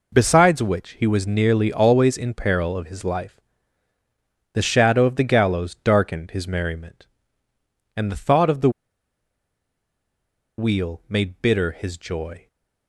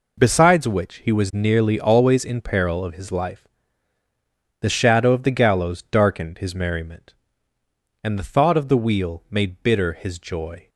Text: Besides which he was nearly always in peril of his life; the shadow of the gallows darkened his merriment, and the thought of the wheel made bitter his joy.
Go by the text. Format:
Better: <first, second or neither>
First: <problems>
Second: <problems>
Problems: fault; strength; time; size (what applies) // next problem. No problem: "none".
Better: second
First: pauses between "the" and "wheel"; strong; at 8.6 s; 1.8 s long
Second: none